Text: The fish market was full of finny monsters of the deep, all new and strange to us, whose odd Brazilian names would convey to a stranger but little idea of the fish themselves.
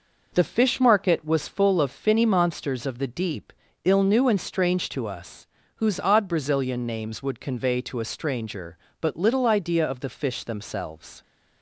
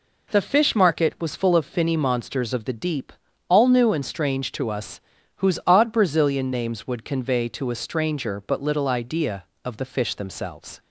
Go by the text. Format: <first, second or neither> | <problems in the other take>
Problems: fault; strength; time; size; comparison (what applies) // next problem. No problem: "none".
second | says "ill" for "all"; at 3.8 s